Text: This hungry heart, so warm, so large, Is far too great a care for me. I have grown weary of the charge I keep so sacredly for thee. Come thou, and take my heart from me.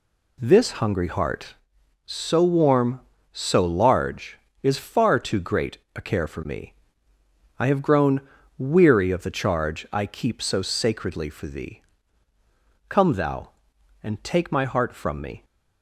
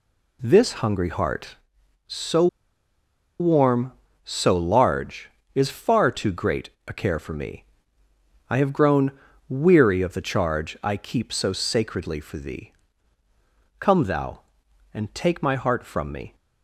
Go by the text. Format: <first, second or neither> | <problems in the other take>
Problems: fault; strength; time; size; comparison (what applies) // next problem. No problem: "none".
first | pauses between "so" and "warm"; noticeable; at 2.4 s; 0.93 s long // pauses between "great" and "a"; slight; at 6.7 s; 0.18 s long; slight in the first // pauses between "grown" and "weary"; slight; at 9.1 s; 0.36 s long; slight in the first